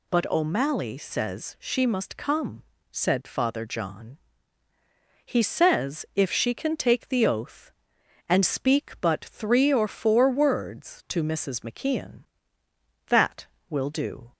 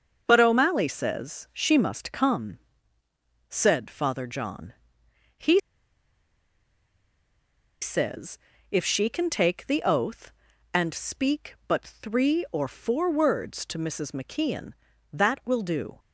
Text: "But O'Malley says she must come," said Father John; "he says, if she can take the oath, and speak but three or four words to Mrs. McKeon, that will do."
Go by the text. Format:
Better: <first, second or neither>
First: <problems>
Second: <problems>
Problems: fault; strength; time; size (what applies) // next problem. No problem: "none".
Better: first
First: none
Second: starts louder than the rest; until 1.2 s; 6.5 dB // pauses between "he" and "says"; strong; at 5.5 s; 2.2 s long